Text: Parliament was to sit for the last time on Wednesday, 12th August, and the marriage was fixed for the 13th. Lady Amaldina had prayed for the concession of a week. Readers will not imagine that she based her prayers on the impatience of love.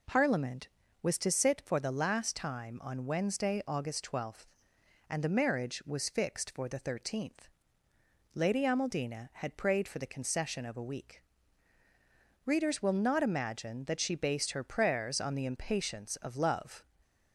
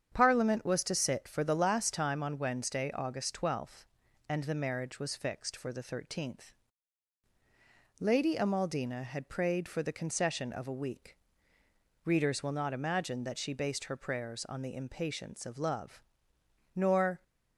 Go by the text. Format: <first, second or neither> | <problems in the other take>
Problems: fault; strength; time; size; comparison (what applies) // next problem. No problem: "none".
first | starts louder than the rest; strong; until 1.1 s; 8.5 dB // goes on to say "Nor"; slight; from 16.7 s on; 0.48 s long